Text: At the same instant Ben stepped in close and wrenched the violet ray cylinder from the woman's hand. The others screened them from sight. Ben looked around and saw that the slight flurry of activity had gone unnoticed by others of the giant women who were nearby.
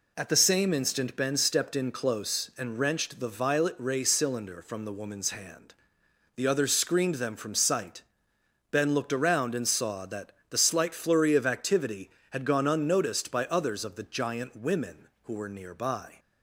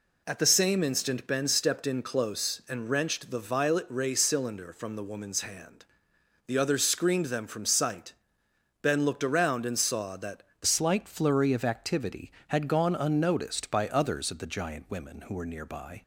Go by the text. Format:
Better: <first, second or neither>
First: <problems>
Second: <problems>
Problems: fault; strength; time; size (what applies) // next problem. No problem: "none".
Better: first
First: pauses between "that" and "the"; slight; at 10.3 s; 0.20 s long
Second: pauses between "that" and "the"; slight; at 10.4 s; 0.20 s long // changes voice at "slight"; from 10.6 s on; 5.4 s long